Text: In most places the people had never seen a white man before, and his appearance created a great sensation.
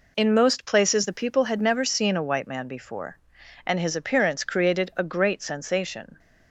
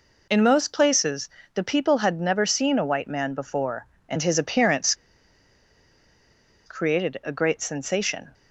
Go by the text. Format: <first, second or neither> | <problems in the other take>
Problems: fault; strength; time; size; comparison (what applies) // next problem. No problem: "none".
first | pauses between "places" and "the"; slight; at 1.2 s; 0.28 s long // pauses between "appearance" and "created"; strong; at 4.9 s; 1.7 s long